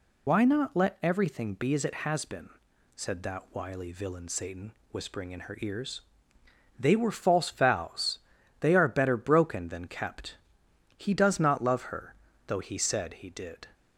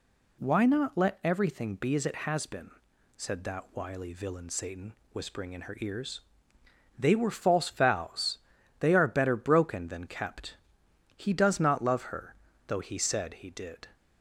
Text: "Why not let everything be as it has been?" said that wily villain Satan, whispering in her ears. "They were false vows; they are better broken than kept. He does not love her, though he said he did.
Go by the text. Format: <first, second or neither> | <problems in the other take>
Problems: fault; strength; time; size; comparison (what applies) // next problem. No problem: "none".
second | loses the start of "Why"; at 0.2 s; 90 ms